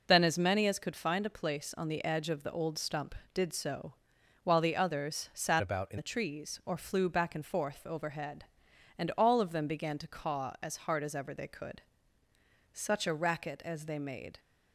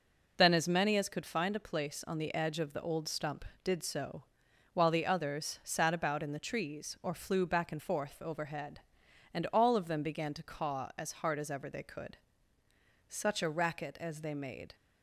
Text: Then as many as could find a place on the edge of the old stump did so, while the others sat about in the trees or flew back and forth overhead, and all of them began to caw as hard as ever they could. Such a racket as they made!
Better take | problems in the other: second | changes voice from "about" to "in"; from 5.6 to 5.9 s; 0.3 s long

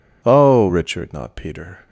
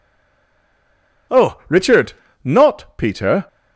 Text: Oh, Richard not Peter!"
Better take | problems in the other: first | stays silent before the first word; noticeable; until 1.3 s; 1.3 s long // pauses between "Richard" and "not"; slight; at 2.1 s; 0.32 s long

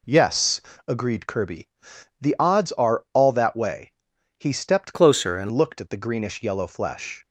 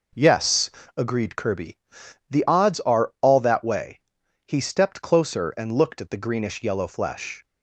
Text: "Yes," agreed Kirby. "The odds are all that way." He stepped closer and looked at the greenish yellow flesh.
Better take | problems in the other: second | changes voice from "closer" to "and"; from 4.9 to 5.4 s; 0.5 s long

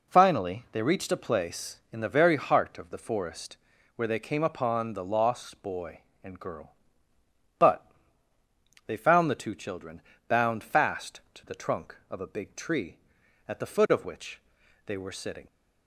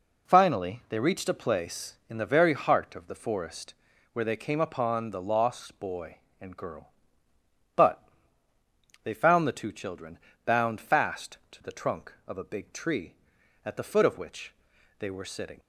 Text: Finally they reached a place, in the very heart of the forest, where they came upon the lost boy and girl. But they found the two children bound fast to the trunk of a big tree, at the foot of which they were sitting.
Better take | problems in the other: neither | pauses between "But" and "they"; the same in both // pauses between "children" and "bound"; slight; the same in both // pauses between "which" and "they"; noticeable; the same in both

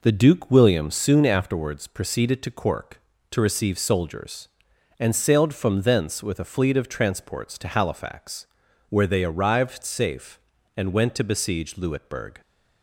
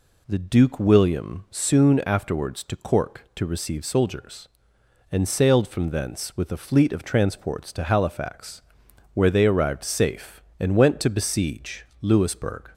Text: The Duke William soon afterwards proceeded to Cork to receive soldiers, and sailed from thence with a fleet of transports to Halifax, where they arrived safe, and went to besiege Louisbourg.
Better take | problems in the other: first | skips "proceeded"; at 2.6 s // pauses between "besiege" and "Louisbourg"; slight; at 11.8 s; 0.16 s long

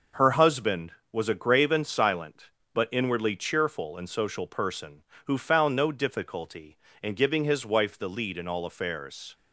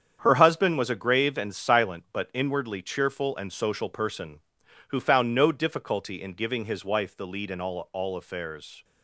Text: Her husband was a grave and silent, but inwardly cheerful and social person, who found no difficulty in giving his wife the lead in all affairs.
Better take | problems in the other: first | starts louder than the rest; strong; until 1.2 s; 8 dB // says "all" twice; at 7.9 s

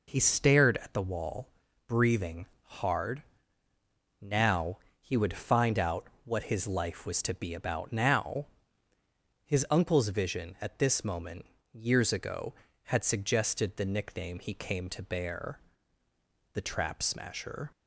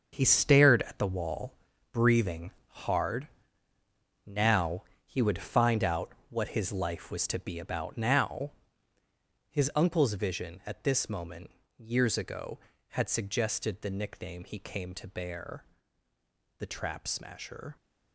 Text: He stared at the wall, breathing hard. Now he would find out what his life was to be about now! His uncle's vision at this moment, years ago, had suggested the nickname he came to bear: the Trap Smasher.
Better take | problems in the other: first | gets quieter; strong; throughout; 9.5 dB // pauses between "breathing" and "hard"; slight; at 2.5 s; 0.16 s long; slight in the first // pauses between "Now" and "he"; slight; at 4.8 s; 0.20 s long; slight in the first // pauses between "out" and "what"; slight; at 6.1 s; 0.18 s long; slight in the first

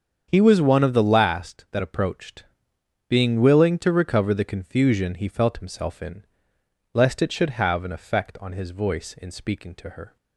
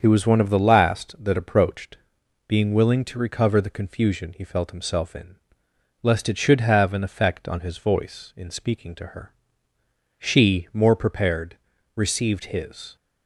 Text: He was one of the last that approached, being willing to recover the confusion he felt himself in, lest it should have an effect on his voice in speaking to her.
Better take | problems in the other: first | starts louder than the rest; strong; until 1.0 s; 7 dB; strong in the first // goes on to say "She more prepared received his"; strong; from 10.1 s on; 2.7 s long

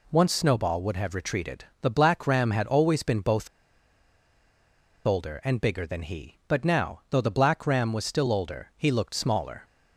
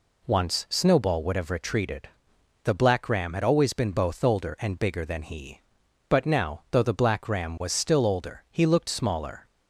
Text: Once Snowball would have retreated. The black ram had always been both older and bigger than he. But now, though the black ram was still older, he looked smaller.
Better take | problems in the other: second | pauses between "both" and "older"; strong; at 3.4 s; 1.5 s long

